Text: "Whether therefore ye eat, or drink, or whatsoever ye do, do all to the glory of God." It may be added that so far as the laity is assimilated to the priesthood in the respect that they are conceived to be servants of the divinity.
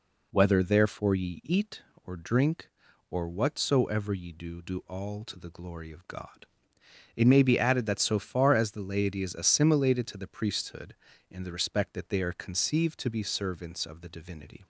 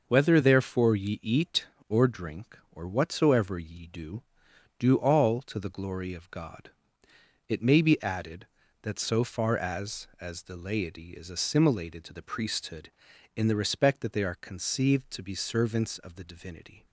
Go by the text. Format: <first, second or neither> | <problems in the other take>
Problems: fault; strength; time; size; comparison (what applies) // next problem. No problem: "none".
first | says "as" twice; at 10.1 s